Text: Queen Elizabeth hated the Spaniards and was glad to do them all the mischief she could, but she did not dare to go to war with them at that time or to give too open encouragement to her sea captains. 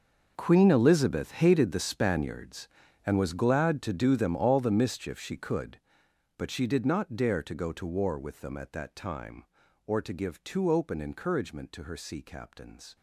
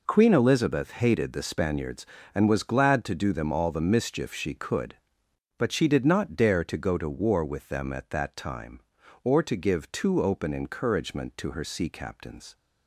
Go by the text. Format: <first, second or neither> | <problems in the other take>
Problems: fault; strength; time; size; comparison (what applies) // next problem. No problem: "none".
second | gets quieter; strong; throughout; 16.5 dB